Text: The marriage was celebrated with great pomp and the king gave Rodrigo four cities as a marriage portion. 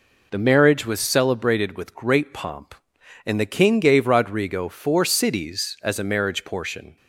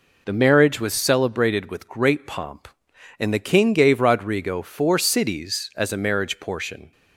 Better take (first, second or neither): neither